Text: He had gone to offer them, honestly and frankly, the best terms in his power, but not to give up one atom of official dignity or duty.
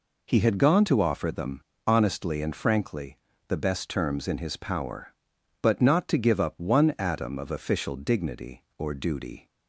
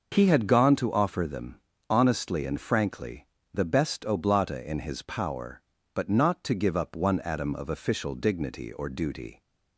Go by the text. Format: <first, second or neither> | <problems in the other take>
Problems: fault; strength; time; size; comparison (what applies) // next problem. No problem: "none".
first | says "oblata" for "terms"; at 4.0 s